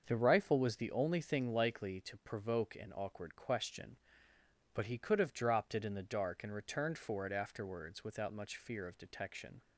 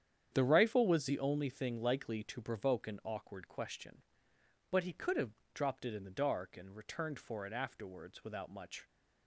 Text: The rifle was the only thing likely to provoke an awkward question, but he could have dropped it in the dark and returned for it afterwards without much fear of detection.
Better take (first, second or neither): first